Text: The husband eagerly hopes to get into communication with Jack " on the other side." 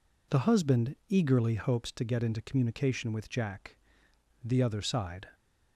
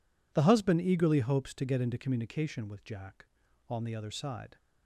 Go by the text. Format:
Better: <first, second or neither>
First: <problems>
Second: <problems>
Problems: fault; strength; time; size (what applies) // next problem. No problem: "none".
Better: second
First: skips "on"; at 4.4 s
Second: none